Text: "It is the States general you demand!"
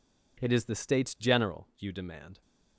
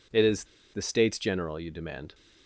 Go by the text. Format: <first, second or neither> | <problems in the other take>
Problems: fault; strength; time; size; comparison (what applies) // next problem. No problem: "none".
first | pauses between "is" and "the"; slight; at 0.4 s; 0.29 s long